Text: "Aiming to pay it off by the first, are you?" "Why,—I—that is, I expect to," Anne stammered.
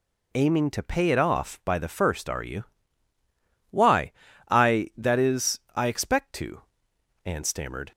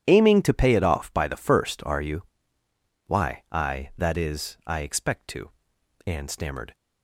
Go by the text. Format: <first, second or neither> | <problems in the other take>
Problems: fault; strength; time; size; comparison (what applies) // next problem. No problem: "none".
neither | none